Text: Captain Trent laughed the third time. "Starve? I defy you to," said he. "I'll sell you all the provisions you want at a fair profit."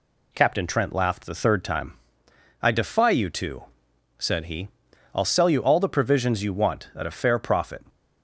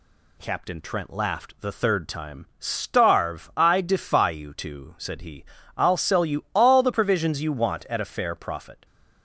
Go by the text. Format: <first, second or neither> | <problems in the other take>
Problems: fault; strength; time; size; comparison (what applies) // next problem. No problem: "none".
second | skips "Starve"; at 2.2 s